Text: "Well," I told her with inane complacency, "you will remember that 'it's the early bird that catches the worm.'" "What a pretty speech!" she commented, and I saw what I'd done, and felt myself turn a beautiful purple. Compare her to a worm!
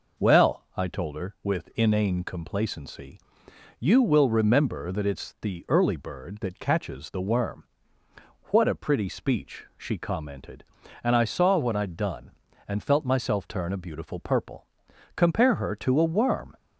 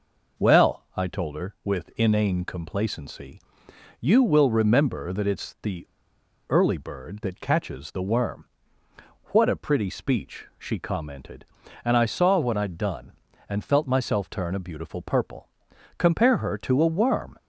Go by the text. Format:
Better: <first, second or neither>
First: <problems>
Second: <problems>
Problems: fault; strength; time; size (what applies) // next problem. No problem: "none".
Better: first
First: none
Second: pauses between "the" and "early"; noticeable; at 5.8 s; 0.62 s long